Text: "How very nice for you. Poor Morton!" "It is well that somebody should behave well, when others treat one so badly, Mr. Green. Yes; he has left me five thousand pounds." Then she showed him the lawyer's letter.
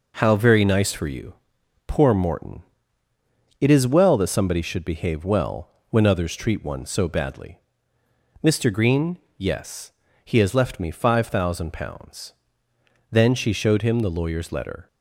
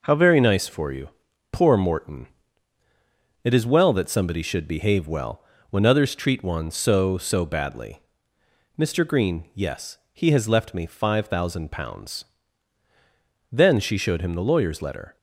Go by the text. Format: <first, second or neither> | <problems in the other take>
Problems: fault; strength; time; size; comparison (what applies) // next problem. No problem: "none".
first | says "so" twice; at 7.1 s